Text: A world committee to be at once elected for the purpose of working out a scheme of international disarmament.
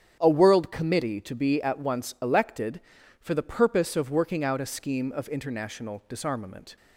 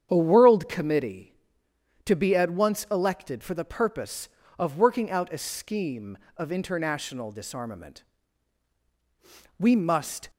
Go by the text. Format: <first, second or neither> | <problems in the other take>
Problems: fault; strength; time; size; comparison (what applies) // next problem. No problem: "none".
first | starts louder than the rest; strong; until 1.1 s; 8.5 dB; strong in the first // goes on to say "We must"; noticeable; from 9.5 s on; 0.70 s long